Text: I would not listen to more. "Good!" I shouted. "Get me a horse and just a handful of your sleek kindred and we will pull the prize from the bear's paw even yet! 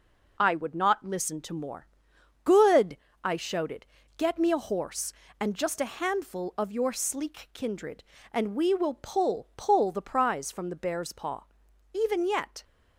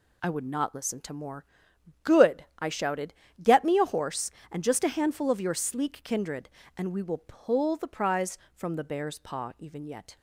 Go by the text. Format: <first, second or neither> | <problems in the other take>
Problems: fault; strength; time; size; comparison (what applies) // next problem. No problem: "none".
second | says "pull" twice; at 9.5 s // pauses between "paw" and "even"; noticeable; at 11.4 s; 0.50 s long